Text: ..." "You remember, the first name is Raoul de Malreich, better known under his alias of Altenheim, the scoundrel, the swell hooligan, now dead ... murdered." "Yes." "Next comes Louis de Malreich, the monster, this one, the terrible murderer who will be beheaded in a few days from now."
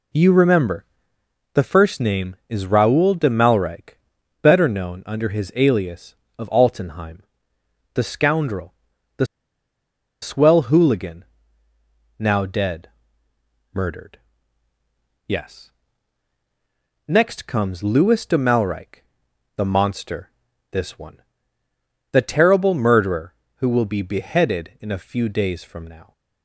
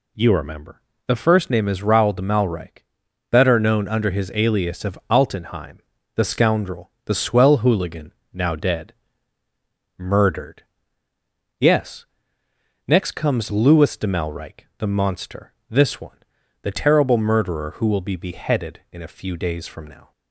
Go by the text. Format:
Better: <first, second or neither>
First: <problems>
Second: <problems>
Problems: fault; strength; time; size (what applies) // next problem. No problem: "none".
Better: second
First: pauses between "the" and "swell"; noticeable; at 9.2 s; 0.97 s long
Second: none